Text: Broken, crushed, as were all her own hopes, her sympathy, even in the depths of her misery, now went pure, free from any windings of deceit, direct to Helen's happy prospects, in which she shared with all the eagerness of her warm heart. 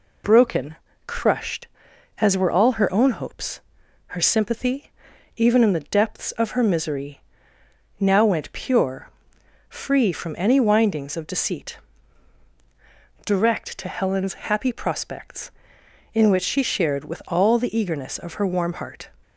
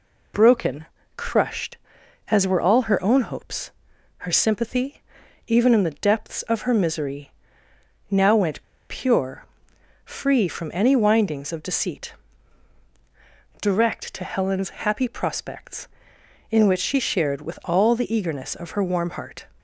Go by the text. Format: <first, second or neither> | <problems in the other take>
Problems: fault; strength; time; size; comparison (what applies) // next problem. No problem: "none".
first | pauses between "went" and "pure"; slight; at 8.6 s; 0.27 s long // pauses between "Helen's" and "happy"; slight; at 14.6 s; 0.16 s long; slight in the first